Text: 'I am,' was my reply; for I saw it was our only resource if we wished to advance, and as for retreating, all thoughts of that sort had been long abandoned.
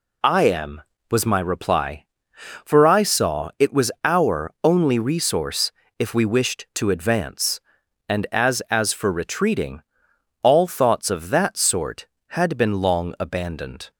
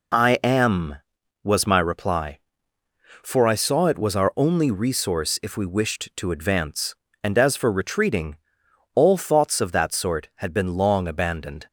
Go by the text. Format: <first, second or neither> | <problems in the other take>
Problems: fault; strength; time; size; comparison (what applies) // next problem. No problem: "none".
second | pauses between "resource" and "if"; slight; at 5.7 s; 0.28 s long // says "as" twice; at 8.6 s